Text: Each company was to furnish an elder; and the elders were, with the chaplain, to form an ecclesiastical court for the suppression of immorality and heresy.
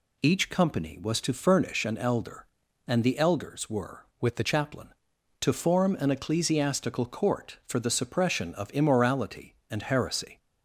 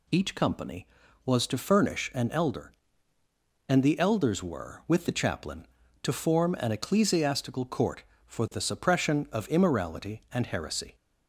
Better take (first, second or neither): second